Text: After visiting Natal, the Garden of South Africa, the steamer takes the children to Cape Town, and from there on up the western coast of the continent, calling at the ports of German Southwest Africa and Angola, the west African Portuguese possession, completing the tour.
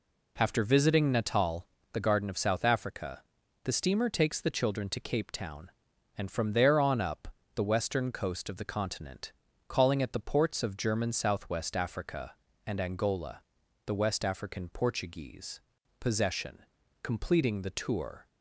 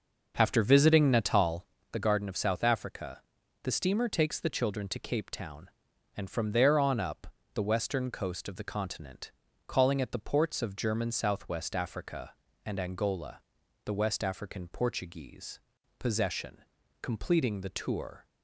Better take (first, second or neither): first